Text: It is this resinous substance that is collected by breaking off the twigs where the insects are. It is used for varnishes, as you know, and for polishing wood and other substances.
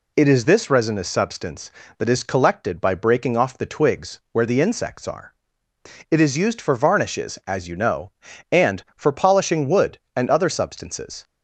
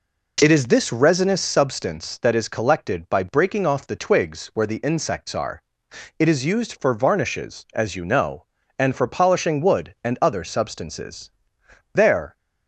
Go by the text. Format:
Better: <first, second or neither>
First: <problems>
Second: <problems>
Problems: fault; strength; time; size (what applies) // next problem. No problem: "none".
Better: first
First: none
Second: goes on to say "There"; slight; from 11.9 s on; 0.44 s long